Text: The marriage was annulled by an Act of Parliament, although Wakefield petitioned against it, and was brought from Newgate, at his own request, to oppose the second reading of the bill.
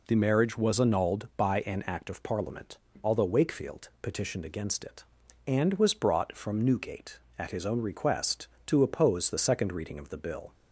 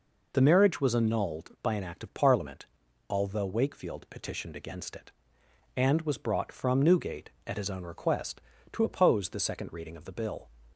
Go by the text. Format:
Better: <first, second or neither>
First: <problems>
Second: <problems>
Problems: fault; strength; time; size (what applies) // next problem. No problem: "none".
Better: neither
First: none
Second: none